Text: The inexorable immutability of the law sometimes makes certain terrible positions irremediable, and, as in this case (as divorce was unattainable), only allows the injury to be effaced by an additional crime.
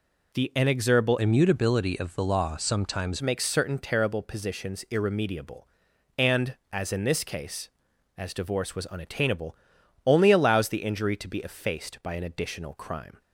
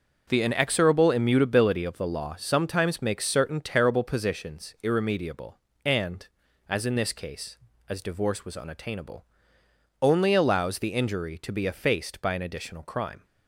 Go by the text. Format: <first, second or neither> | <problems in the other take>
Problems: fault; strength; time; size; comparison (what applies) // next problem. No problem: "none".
second | changes voice from "immutability" to "sometimes"; from 1.1 to 3.2 s; 2.1 s long